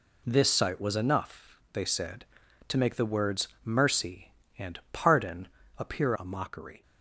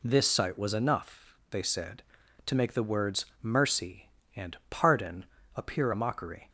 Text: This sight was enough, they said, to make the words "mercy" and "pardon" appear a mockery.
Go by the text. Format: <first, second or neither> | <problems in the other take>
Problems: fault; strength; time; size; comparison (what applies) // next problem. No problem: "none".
second | pauses between "words" and "mercy"; slight; at 3.4 s; 0.16 s long; slight in the second // pauses between "pardon" and "appear"; slight; at 5.4 s; 0.28 s long; slight in the second // changes voice at "a"; from 6.1 s on; 0.7 s long